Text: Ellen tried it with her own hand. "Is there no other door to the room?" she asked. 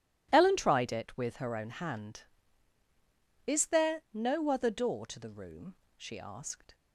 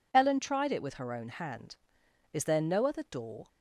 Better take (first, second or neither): first